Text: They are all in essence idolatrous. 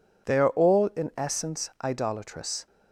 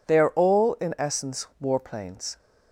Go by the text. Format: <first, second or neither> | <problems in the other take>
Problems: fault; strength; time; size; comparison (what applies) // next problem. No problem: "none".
first | says "warplanes" for "idolatrous"; at 1.6 s